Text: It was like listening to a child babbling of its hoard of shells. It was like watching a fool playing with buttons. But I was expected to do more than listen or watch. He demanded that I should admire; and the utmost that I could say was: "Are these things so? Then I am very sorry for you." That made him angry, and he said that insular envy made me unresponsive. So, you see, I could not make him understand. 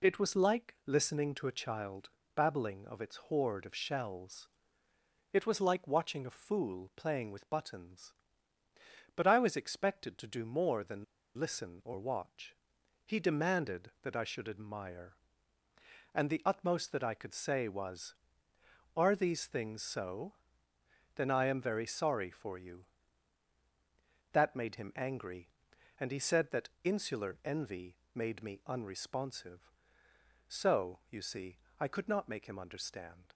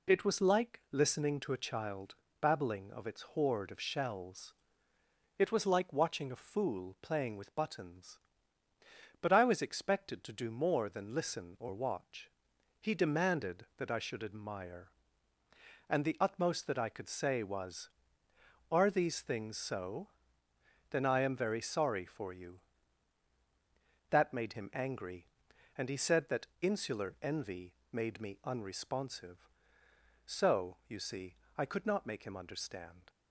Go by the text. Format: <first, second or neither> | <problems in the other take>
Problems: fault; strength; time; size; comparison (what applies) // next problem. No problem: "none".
second | pauses between "child" and "babbling"; slight; at 2.0 s; 0.26 s long; slight in the second // pauses between "than" and "listen"; slight; at 11.0 s; 0.33 s long // pauses between "envy" and "made"; slight; at 27.9 s; 0.18 s long; slight in the second